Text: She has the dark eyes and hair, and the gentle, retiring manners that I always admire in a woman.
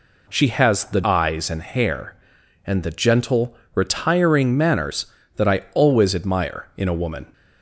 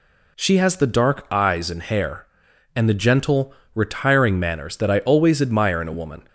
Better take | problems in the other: second | skips "dark"; at 1.0 s

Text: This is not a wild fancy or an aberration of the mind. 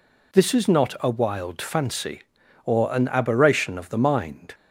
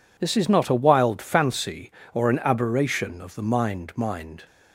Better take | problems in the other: first | says "mind" twice; at 3.9 s

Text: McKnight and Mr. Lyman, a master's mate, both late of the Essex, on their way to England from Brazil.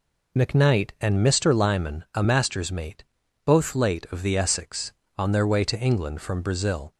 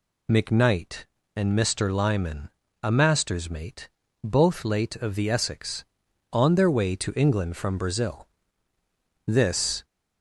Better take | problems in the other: first | goes on to say "This"; from 9.2 s on; 0.58 s long

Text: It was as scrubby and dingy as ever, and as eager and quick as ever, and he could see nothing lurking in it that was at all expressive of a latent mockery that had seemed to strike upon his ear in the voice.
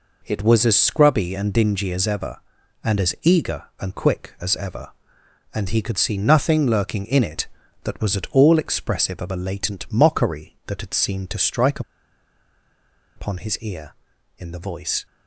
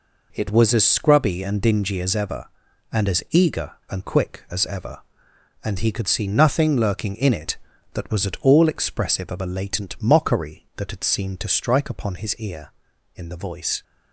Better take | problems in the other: second | pauses between "strike" and "upon"; strong; at 11.8 s; 1.3 s long

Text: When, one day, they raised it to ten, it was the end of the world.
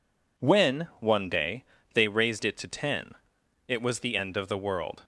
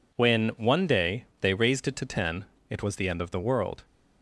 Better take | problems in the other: neither | none

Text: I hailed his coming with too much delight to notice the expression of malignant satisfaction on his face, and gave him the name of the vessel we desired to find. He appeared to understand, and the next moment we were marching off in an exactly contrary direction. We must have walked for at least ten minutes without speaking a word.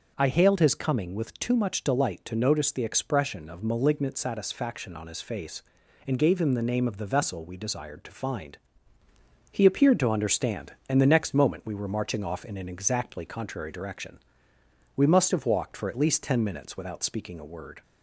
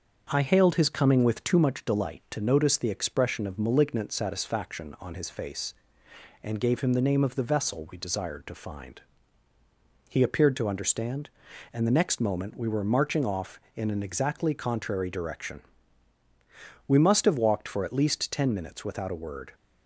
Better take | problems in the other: first | starts louder than the rest; until 1.3 s; 6.5 dB; also in the first // skips "speaking"; at 19.1 s

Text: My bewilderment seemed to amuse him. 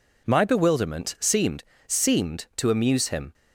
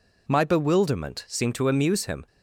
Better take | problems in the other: second | says "seemed" twice; at 1.8 s

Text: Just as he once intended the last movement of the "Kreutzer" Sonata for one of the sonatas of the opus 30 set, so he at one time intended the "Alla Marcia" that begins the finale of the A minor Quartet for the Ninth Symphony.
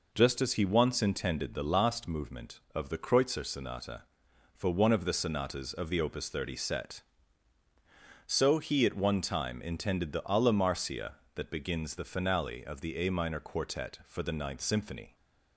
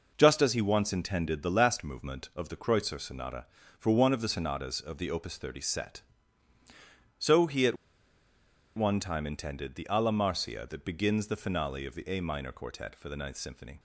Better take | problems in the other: first | pauses between "at" and "one"; at 7.7 s; 1.0 s long

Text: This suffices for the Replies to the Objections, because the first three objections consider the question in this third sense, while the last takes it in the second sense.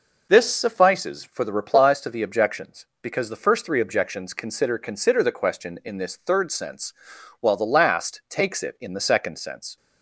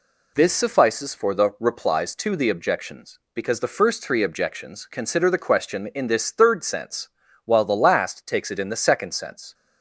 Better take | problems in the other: second | says "consider" twice; at 4.7 s

